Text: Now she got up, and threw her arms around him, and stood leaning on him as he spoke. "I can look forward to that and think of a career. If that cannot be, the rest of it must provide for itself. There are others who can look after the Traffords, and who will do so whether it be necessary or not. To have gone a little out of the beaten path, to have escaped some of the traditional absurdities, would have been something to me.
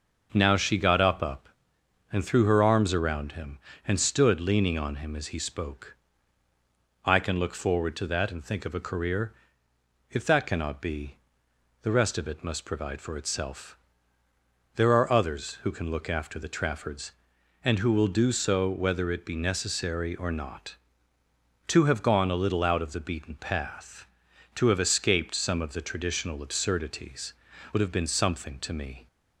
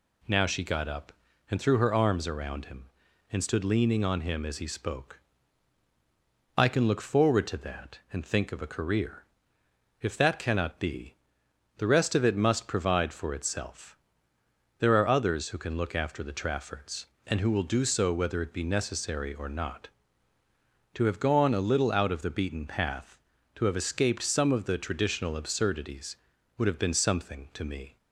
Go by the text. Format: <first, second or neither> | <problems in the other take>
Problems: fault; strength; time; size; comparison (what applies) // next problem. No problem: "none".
second | starts louder than the rest; until 1.3 s; 6 dB // says "up" twice; at 1.2 s